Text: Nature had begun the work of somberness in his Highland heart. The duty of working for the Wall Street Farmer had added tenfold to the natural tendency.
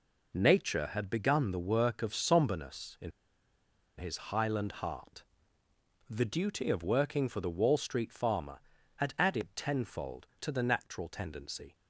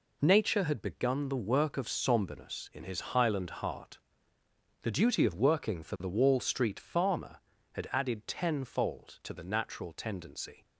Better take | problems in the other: second | pauses between "in" and "his"; noticeable; at 3.1 s; 0.88 s long

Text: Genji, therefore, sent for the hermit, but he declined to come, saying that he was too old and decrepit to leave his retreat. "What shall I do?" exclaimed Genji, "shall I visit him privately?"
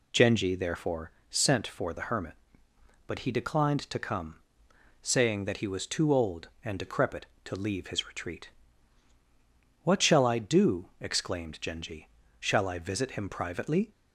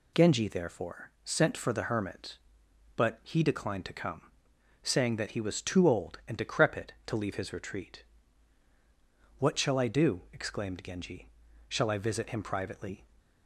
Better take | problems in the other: neither | none

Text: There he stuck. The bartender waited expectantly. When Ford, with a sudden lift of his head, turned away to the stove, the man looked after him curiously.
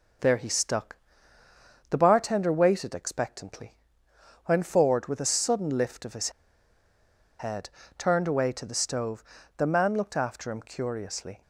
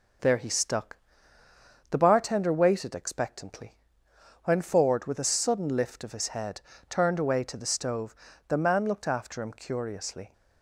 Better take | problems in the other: second | pauses between "his" and "head"; at 6.3 s; 1.0 s long

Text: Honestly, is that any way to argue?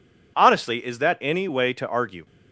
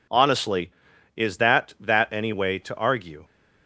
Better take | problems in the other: first | says "that" twice; at 1.7 s

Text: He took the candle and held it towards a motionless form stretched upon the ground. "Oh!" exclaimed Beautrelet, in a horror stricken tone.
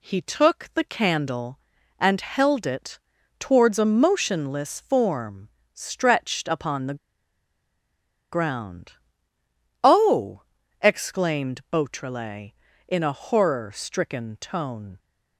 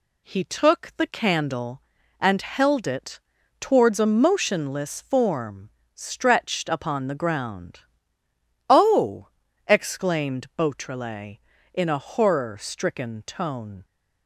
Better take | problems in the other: second | pauses between "it" and "towards"; at 2.9 s; 0.40 s long; also in the second // pauses between "form" and "stretched"; slight; at 5.4 s; 0.26 s long; slight in the second // pauses between "the" and "ground"; strong; at 6.9 s; 1.3 s long

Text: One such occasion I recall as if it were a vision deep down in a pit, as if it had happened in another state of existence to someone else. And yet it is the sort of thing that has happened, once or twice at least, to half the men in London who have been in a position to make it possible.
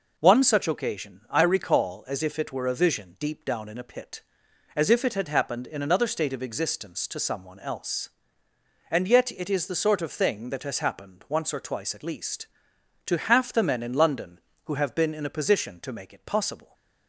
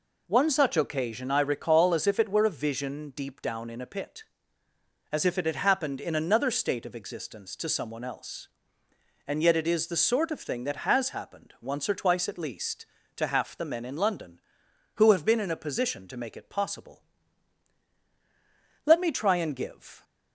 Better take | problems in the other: first | goes on to say "Let me try and give"; noticeable; from 18.8 s on; 1.1 s long

